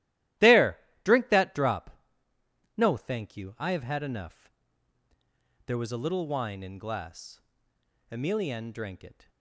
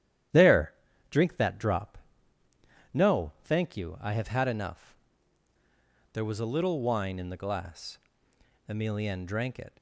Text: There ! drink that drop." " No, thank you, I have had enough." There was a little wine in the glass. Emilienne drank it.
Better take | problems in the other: second | starts louder than the rest; strong; until 1.6 s; 15 dB; strong in the second // skips "the"; at 6.7 s

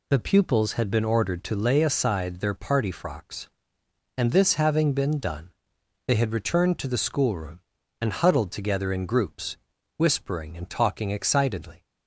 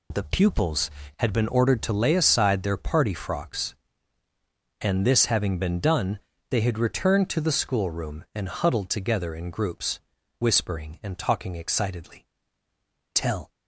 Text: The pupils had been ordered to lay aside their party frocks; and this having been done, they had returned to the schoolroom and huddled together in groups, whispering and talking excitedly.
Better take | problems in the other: first | goes on to say "Tell"; slight; from 13.1 s on; 0.38 s long

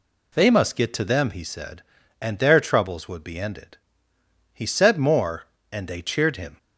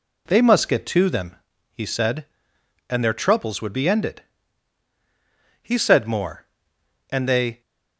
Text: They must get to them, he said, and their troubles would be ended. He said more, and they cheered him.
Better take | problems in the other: first | stops before "cheered him"; at 7.6 s

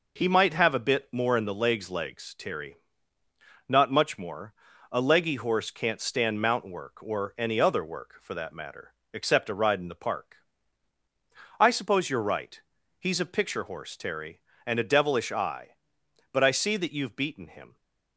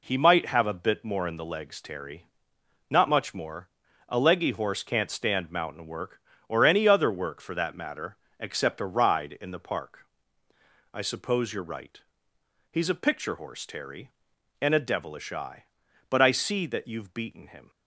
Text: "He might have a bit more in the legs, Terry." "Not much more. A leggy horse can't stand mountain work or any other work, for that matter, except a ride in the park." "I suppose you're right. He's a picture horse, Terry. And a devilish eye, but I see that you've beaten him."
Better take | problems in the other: second | says "legs" twice; at 1.9 s

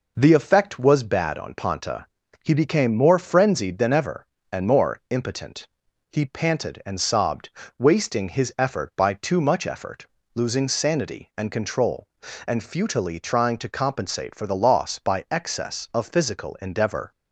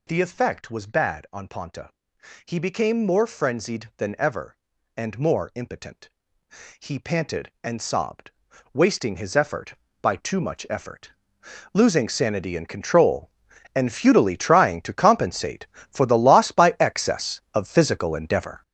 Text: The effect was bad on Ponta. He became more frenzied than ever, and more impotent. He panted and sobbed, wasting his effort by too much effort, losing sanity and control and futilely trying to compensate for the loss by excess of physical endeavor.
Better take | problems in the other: first | gets louder; strong; throughout; 8 dB

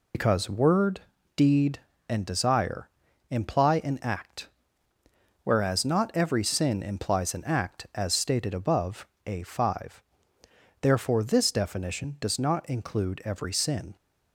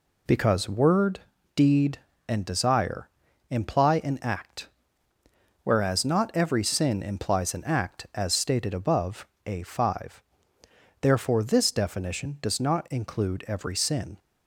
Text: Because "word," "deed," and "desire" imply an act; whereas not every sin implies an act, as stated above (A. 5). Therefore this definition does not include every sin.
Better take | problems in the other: second | loses the start of "Because"; at 0.1 s; 75 ms // pauses between "desire" and "imply"; at 2.8 s; 0.40 s long; also in the second

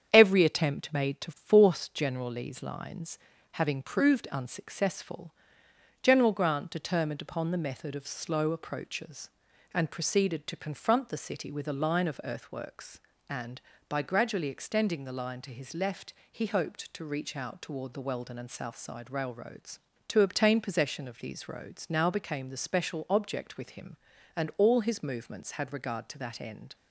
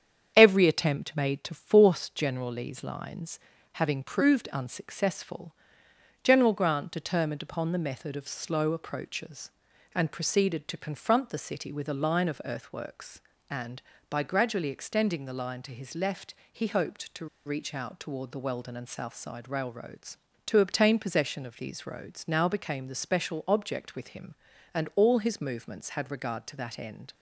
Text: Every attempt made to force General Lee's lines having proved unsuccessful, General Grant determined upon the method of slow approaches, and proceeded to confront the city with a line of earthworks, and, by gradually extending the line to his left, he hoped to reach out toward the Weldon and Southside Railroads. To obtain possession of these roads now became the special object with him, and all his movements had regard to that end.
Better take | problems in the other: first | starts louder than the rest; strong; until 1.3 s; 8 dB; strong in the first // pauses between "lines" and "having"; slight; at 3.3 s; 0.36 s long; slight in the first // pauses between "to" and "reach"; slight; at 17.2 s; 0.19 s long

